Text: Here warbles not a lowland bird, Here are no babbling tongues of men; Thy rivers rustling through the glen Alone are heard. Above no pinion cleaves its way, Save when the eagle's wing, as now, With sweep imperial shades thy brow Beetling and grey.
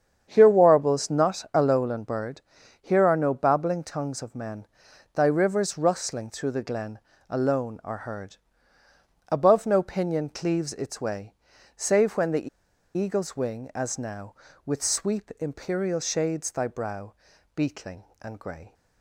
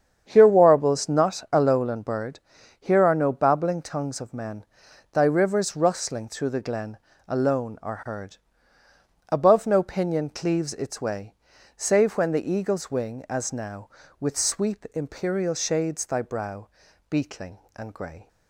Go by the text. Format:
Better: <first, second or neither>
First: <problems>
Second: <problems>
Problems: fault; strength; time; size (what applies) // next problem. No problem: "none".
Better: second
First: starts louder than the rest; strong; until 1.3 s; 8 dB // pauses between "glen" and "Alone"; slight; at 6.9 s; 0.30 s long // pauses between "the" and "eagle's"; noticeable; at 12.4 s; 0.48 s long // pauses between "brow" and "Beetling"; at 17.1 s; 0.40 s long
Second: starts louder than the rest; strong; until 1.2 s; 8 dB // pauses between "glen" and "Alone"; slight; at 6.9 s; 0.30 s long // pauses between "brow" and "Beetling"; at 16.6 s; 0.40 s long